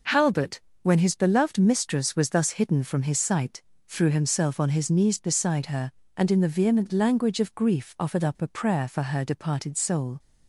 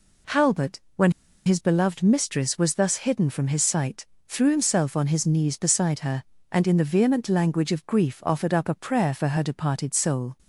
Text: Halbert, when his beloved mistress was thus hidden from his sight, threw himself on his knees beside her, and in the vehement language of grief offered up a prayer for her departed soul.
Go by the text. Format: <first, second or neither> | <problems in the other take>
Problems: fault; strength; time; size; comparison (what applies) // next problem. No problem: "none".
first | pauses between "when" and "his"; slight; at 1.1 s; 0.33 s long